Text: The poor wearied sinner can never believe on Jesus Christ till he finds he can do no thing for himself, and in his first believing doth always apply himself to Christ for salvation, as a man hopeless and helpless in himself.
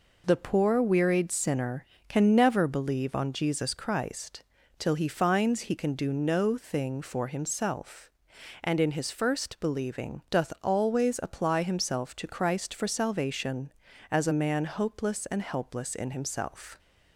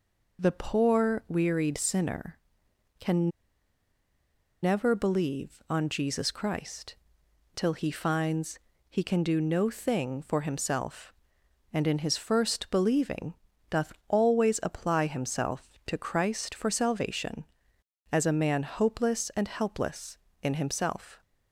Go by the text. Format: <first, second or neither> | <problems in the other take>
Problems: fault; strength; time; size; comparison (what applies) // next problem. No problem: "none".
first | pauses between "can" and "never"; strong; at 3.2 s; 1.3 s long // pauses between "Christ" and "till"; noticeable; at 6.9 s; 0.60 s long; slight in the first // pauses between "finds" and "he"; slight; at 8.5 s; 0.30 s long // pauses between "believing" and "doth"; at 13.3 s; 0.38 s long // pauses between "doth" and "always"; slight; at 13.9 s; 0.16 s long